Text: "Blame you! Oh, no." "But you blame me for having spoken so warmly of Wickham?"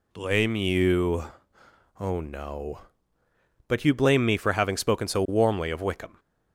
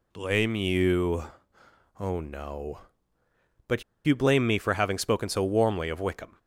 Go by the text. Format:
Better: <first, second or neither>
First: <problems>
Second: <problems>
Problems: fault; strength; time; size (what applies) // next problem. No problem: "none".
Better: first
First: none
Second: pauses between "But" and "you"; slight; at 3.8 s; 0.22 s long